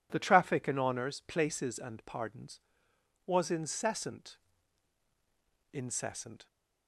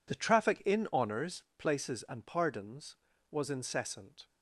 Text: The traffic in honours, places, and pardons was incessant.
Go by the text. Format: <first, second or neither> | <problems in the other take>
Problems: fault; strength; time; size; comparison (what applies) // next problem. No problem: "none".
second | says "incessant" twice; at 5.7 s